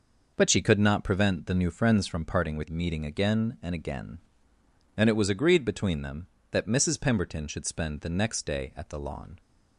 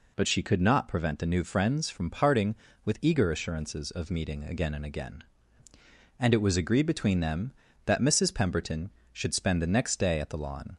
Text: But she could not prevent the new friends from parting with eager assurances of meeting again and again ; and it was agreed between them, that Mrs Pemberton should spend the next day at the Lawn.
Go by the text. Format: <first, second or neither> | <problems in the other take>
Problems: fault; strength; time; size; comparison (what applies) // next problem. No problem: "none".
second | skips "eager assurances of"; at 2.6 s